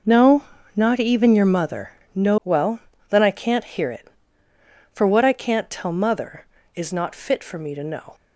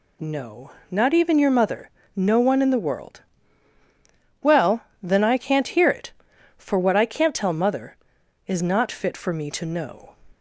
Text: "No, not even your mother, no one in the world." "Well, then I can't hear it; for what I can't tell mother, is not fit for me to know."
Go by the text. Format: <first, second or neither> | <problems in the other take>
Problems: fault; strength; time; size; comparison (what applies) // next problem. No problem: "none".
second | skips "one in the world"; at 2.4 s